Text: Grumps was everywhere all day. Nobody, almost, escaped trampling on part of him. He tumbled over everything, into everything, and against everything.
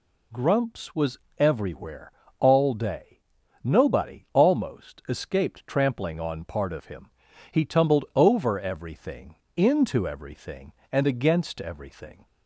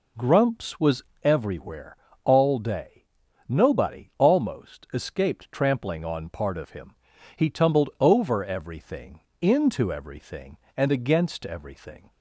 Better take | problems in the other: first | starts louder than the rest; slight; until 1.2 s; 3.5 dB // pauses between "was" and "everywhere"; slight; at 1.0 s; 0.20 s long; slight in the first // pauses between "everywhere" and "all"; slight; at 1.9 s; 0.26 s long; slight in the first

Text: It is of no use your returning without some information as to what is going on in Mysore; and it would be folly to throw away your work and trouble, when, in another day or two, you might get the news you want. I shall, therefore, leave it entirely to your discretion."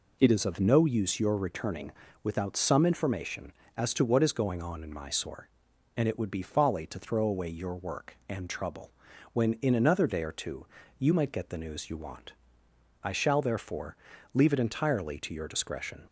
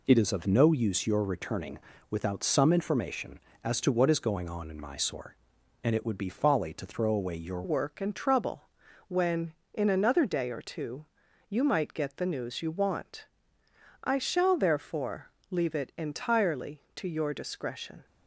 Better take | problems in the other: first | pauses between "returning" and "without"; slight; at 1.7 s; 0.32 s long; slight in the first // changes voice at "work"; from 7.6 s on; 10.4 s long

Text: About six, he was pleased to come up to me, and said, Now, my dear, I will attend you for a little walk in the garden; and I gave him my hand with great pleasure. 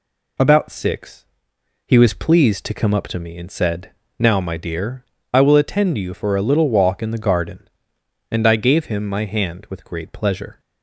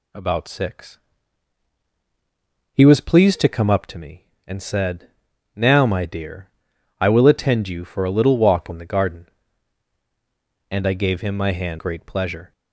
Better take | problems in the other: first | skips "with"; at 11.7 s

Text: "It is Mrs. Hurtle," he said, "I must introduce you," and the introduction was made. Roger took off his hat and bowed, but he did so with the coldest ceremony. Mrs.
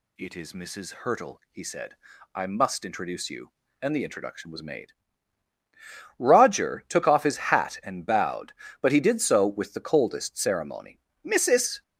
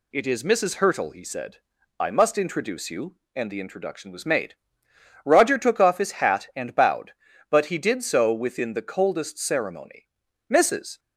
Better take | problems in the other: first | says "within" for "with"; at 8.3 s

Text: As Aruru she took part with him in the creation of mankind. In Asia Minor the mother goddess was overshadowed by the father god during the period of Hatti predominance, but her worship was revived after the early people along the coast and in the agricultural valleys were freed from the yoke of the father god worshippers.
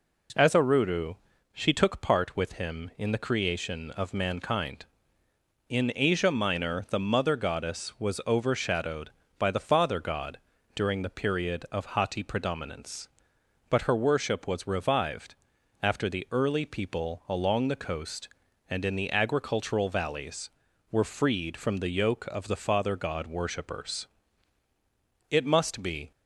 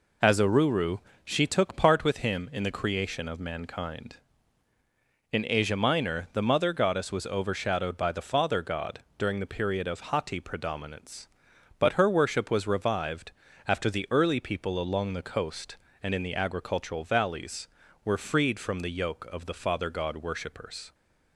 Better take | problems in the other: second | pauses between "Aruru" and "she"; at 1.1 s; 0.38 s long; slight in the second // pauses between "god" and "during"; slight; at 10.3 s; 0.36 s long; slight in the second // pauses between "revived" and "after"; noticeable; at 15.3 s; 0.48 s long; slight in the second // goes on to say "It must be"; noticeable; from 25.2 s on; 0.82 s long

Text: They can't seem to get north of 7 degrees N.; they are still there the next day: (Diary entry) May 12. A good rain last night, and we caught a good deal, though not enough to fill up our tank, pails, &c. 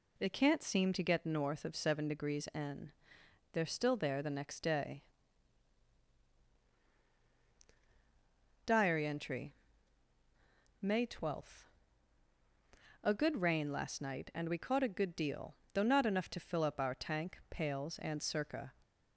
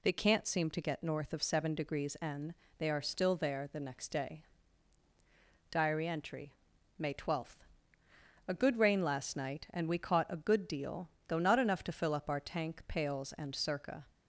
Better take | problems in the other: neither | none

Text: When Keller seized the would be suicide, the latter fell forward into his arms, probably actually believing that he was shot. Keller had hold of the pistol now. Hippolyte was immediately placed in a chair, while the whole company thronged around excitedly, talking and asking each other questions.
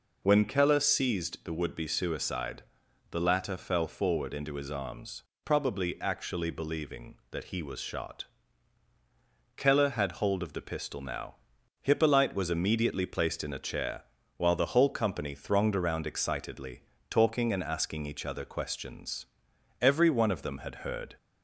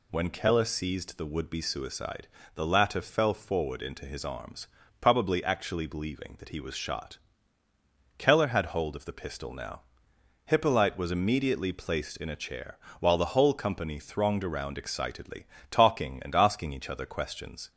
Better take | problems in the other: second | goes on to say "Every one of them had heard"; from 19.8 s on; 1.3 s long

